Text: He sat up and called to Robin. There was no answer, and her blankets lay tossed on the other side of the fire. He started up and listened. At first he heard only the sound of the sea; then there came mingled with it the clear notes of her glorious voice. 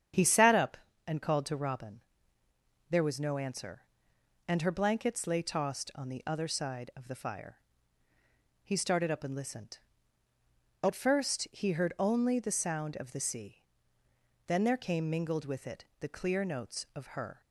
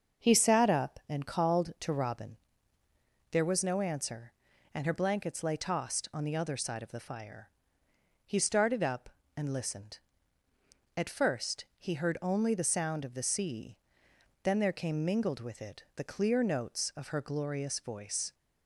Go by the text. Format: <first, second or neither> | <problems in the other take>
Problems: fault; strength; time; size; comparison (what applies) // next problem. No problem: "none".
second | starts louder than the rest; strong; until 1.4 s; 8.5 dB; also in the second // pauses between "it" and "the"; slight; at 15.8 s; 0.16 s long // stops before "glorious voice"; at 17.4 s